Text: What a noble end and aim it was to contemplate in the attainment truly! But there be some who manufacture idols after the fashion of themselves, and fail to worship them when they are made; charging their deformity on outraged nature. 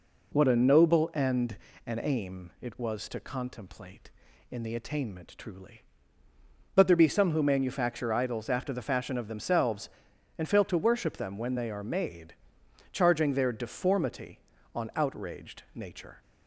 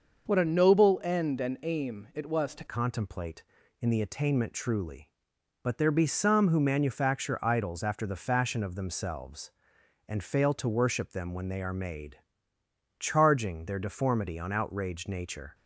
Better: first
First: none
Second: starts louder than the rest; noticeable; until 1.3 s; 6 dB // changes voice at "contemplate"; from 2.6 s on; 12.9 s long

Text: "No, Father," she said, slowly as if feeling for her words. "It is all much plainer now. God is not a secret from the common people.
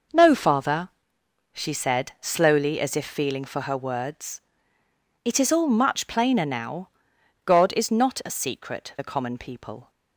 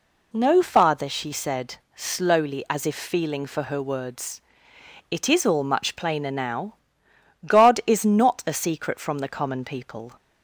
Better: second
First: skips "from"; at 8.9 s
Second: none

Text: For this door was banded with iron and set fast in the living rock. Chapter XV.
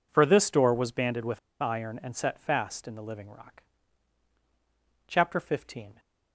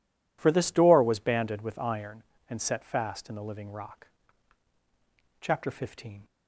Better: second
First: pauses between "with" and "iron"; slight; at 1.3 s; 0.22 s long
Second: none

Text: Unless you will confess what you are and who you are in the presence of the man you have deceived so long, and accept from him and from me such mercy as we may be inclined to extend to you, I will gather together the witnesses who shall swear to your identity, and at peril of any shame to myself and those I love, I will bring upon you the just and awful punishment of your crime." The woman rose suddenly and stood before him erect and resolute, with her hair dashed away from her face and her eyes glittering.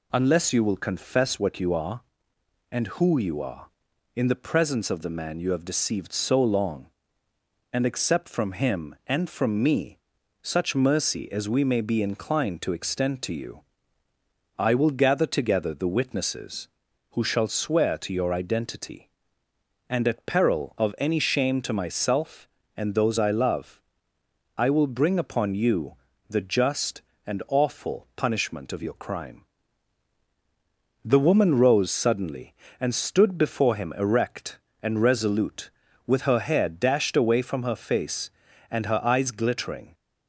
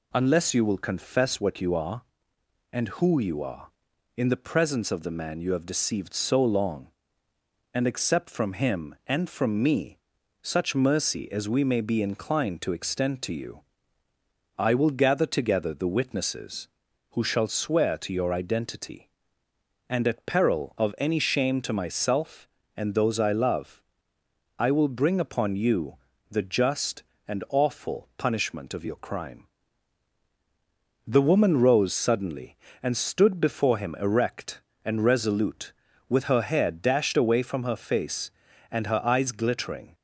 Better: neither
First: pauses between "me" and "such"; at 9.9 s; 0.44 s long // pauses between "you" and "the"; slight; at 25.9 s; 0.30 s long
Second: pauses between "me" and "such"; at 9.9 s; 0.44 s long // pauses between "you" and "the"; slight; at 25.9 s; 0.30 s long

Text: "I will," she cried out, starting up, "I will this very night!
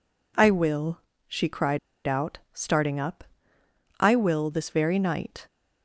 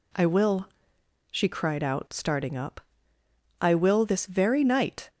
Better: second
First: pauses between "cried" and "out"; slight; at 1.7 s; 0.27 s long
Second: none

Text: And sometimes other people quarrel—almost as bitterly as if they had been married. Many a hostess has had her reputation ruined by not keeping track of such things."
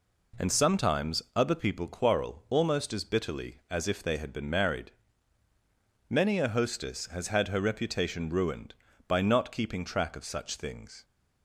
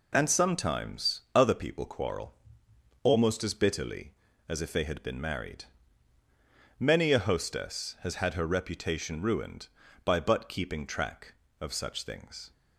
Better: first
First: none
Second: says "but" for "not"; at 10.1 s

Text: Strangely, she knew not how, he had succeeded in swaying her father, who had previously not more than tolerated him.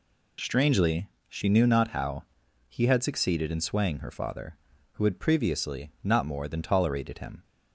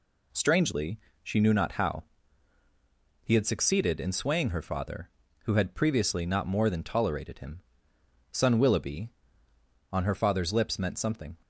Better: first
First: none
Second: goes on to say "Son Willoughby on her father's lips meant something"; strong; from 8.3 s on; 3.0 s long

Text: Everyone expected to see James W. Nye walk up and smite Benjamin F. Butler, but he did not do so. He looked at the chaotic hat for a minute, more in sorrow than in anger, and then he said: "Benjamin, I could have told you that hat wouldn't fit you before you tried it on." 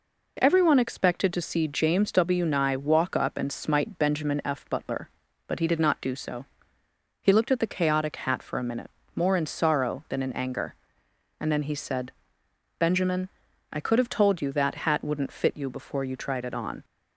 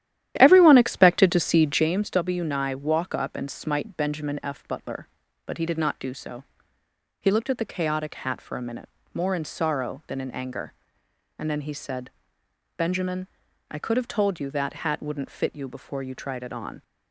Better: first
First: none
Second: starts louder than the rest; strong; until 1.9 s; 12 dB

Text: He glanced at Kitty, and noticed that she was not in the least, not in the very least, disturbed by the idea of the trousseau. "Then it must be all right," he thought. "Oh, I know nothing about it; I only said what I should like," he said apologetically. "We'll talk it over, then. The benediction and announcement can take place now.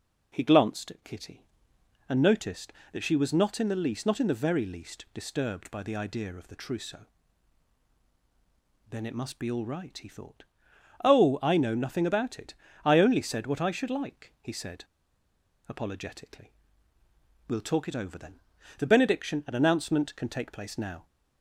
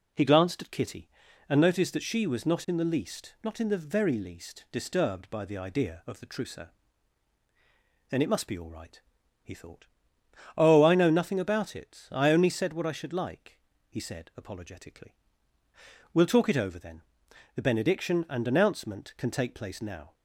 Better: second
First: pauses between "said" and "apologetically"; noticeable; at 14.8 s; 0.82 s long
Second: none

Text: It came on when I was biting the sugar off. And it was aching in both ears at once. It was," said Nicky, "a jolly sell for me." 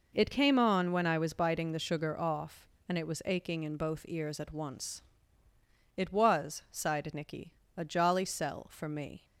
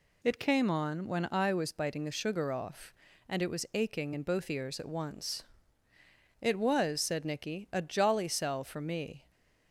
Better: second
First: says "sighed" for "said"; at 6.7 s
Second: none

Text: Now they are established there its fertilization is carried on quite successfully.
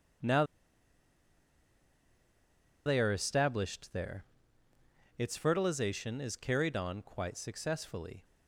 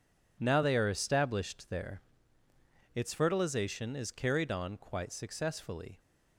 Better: second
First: pauses between "Now" and "they"; strong; at 0.4 s; 2.4 s long // pauses between "there" and "its"; noticeable; at 4.2 s; 0.92 s long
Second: pauses between "there" and "its"; noticeable; at 2.0 s; 0.92 s long

